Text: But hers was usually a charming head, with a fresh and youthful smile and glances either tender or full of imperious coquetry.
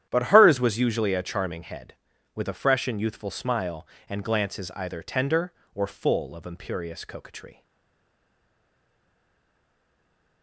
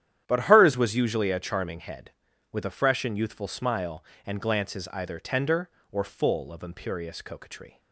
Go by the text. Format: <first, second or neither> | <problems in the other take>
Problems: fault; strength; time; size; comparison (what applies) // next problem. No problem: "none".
second | starts louder than the rest; strong; until 1.1 s; 10.5 dB; strong in the second // stays silent after the last word; strong; from 7.6 s on; 2.8 s long